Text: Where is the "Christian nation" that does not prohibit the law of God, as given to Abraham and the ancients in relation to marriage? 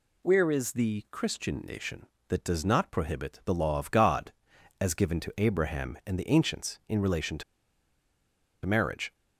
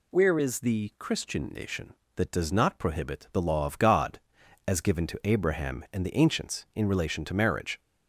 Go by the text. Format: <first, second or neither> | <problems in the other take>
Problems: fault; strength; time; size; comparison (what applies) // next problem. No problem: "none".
second | pauses between "to" and "marriage"; at 7.4 s; 1.2 s long